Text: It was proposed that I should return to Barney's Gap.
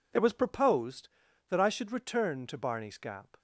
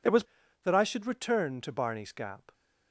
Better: first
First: none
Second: skips "proposed"; at 0.4 s

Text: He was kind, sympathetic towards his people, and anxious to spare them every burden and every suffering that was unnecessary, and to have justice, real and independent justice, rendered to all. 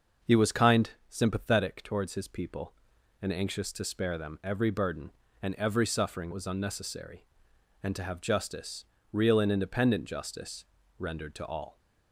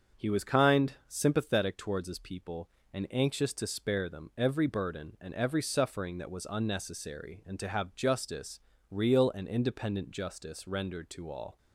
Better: second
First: starts louder than the rest; until 1.4 s; 6 dB // skips "that"; at 6.3 s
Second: starts louder than the rest; until 1.2 s; 7 dB

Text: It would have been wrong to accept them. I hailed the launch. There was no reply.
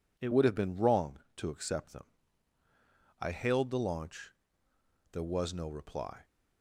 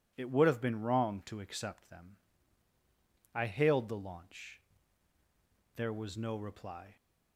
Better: second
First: changes voice at "would"; from 0.3 s on; 5.9 s long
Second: none

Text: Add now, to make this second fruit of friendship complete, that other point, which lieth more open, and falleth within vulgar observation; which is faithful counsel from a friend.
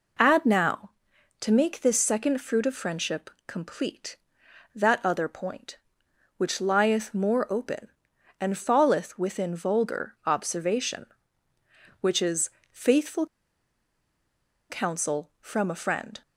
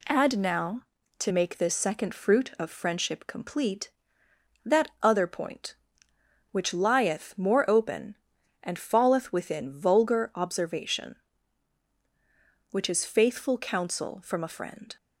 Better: second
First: pauses between "friendship" and "complete"; slight; at 3.2 s; 0.16 s long // pauses between "is" and "faithful"; slight; at 12.4 s; 0.22 s long // pauses between "faithful" and "counsel"; strong; at 13.2 s; 1.4 s long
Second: none

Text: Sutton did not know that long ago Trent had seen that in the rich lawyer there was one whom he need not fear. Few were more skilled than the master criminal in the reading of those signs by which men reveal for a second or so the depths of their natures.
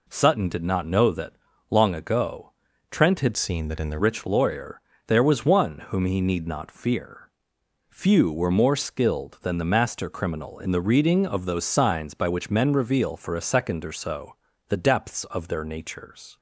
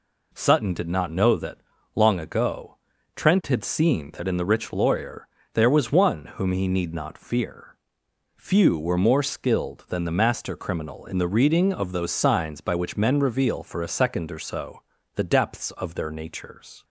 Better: second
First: pauses between "that" and "long"; slight; at 1.3 s; 0.36 s long // pauses between "ago" and "Trent"; at 2.5 s; 0.40 s long // changes voice from "seen" to "the"; from 3.3 to 3.9 s; 0.6 s long // pauses between "lawyer" and "there"; slight; at 4.8 s; 0.26 s long // pauses between "so" and "the"; slight; at 14.3 s; 0.32 s long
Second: pauses between "that" and "long"; slight; at 1.5 s; 0.36 s long // pauses between "ago" and "Trent"; at 2.7 s; 0.40 s long // pauses between "lawyer" and "there"; slight; at 5.2 s; 0.26 s long // pauses between "so" and "the"; slight; at 14.8 s; 0.32 s long

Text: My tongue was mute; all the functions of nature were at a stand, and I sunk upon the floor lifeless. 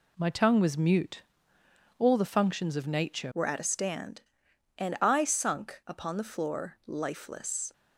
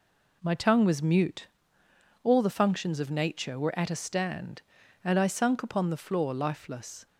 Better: second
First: changes voice at "were"; from 3.3 s on; 4.4 s long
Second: none

